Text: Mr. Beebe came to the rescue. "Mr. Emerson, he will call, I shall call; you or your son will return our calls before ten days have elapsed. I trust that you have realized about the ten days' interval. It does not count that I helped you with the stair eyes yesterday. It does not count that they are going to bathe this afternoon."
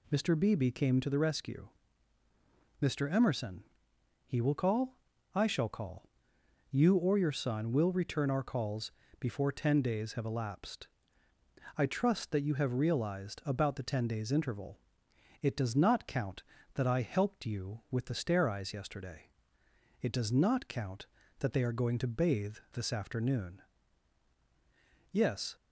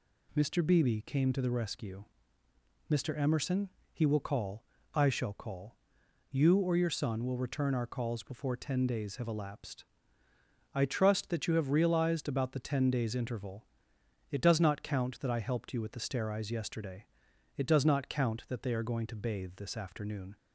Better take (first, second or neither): second